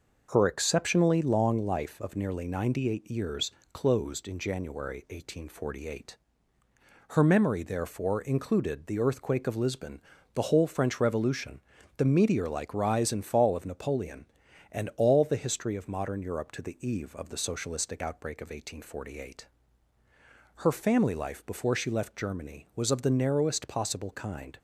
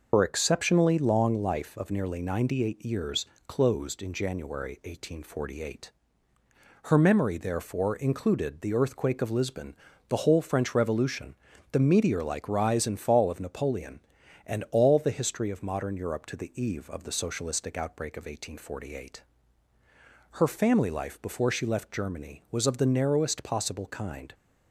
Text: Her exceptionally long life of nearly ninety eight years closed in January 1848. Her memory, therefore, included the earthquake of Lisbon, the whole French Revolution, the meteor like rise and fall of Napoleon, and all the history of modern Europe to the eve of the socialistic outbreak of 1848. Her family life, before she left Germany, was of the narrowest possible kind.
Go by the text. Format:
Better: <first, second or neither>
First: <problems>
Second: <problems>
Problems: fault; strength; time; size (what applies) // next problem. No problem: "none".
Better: first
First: pauses between "years" and "closed"; slight; at 3.4 s; 0.24 s long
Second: loses the start of "Her"; at 0.1 s; 85 ms // pauses between "years" and "closed"; slight; at 3.2 s; 0.24 s long